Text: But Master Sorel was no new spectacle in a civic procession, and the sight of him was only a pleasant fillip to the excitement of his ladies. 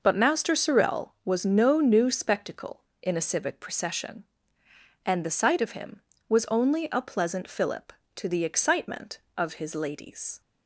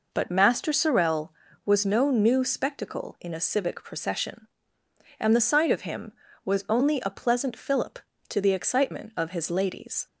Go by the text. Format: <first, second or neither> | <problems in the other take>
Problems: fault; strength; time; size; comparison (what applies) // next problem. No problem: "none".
neither | none